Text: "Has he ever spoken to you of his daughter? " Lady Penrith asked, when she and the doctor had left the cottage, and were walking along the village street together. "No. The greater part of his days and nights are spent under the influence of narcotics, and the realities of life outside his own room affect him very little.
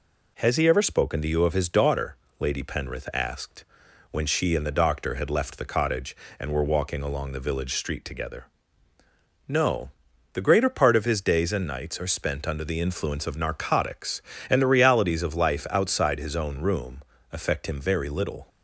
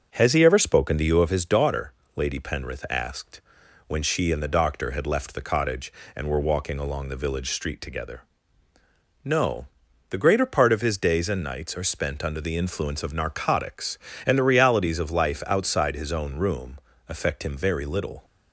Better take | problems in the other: first | starts louder than the rest; noticeable; until 1.3 s; 6 dB // pauses between "room" and "affect"; slight; at 16.7 s; 0.28 s long; slight in the first

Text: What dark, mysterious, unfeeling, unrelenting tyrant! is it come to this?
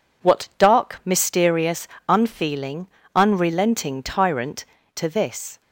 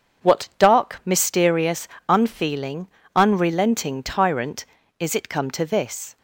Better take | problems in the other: second | skips "is it come"; at 4.8 s

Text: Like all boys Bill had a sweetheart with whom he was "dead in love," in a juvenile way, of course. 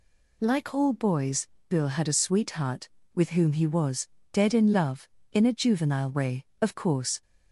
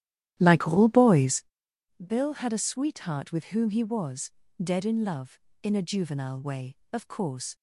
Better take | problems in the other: first | starts louder than the rest; strong; until 1.6 s; 12.5 dB // pauses between "boys" and "Bill"; noticeable; at 1.4 s; 0.62 s long; slight in the first // pauses between "was" and "dead"; slight; at 4.3 s; 0.30 s long; slight in the first

